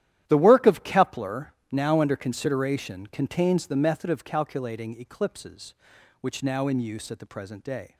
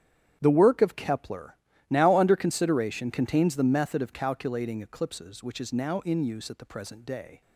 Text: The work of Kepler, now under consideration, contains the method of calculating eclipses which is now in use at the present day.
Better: second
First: starts louder than the rest; strong; until 1.2 s; 12 dB // skips "is"; at 6.4 s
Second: starts louder than the rest; strong; until 1.4 s; 9.5 dB

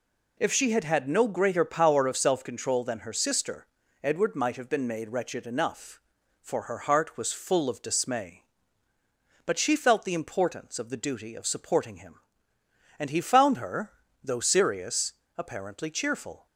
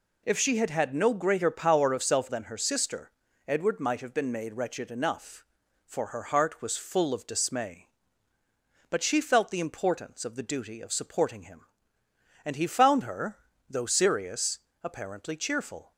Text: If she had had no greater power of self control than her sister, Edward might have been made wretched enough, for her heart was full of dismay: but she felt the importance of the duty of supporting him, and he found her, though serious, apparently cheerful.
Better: first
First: none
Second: skips "control"; at 2.2 s

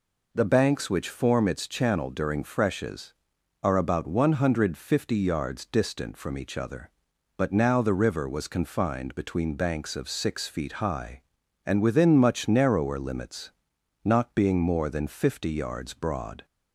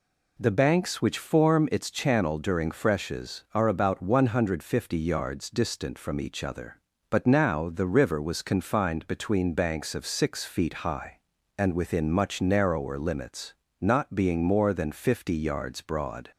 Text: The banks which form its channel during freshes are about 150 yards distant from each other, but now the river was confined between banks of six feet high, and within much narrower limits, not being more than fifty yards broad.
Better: neither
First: none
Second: none

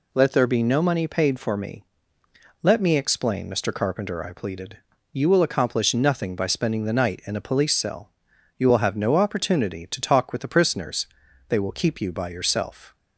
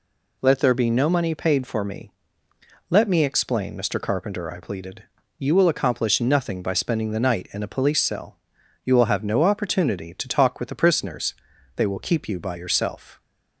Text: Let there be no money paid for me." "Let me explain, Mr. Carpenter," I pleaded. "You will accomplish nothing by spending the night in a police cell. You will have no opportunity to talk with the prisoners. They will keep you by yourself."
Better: neither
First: none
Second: none

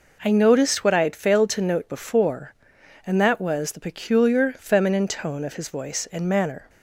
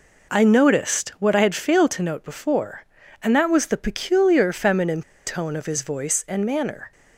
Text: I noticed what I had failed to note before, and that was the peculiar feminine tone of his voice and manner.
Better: first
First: none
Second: pauses between "feminine" and "tone"; slight; at 5.0 s; 0.25 s long

